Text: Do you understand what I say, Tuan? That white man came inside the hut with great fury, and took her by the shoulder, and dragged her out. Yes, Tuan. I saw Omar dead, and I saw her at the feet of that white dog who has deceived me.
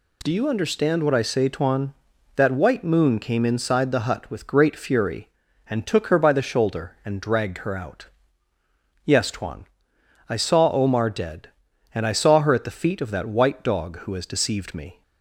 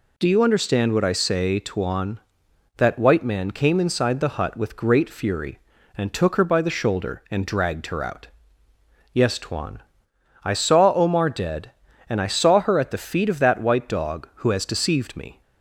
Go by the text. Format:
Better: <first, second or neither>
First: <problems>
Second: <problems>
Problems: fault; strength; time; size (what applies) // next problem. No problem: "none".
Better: second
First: says "moon" for "man"; at 2.8 s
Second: none